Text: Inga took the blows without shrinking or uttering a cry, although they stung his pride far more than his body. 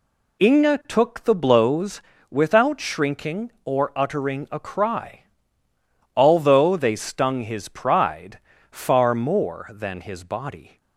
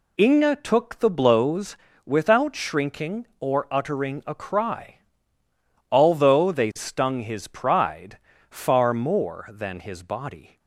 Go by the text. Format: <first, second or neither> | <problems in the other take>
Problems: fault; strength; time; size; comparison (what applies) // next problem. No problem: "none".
neither | pauses between "blows" and "without"; slight; the same in both // pauses between "pride" and "far"; slight; the same in both